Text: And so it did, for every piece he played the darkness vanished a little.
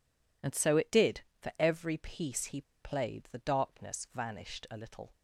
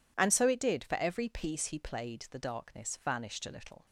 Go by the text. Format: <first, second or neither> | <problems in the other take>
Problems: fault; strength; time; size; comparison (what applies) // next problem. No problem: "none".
second | pauses between "he" and "played"; slight; at 2.6 s; 0.20 s long